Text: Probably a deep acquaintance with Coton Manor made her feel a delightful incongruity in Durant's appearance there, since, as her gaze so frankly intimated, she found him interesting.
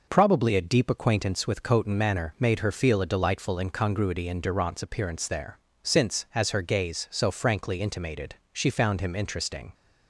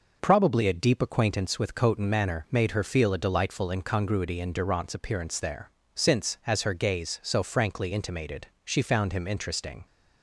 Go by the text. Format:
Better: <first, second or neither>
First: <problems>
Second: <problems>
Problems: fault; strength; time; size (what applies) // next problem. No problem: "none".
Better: neither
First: none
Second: none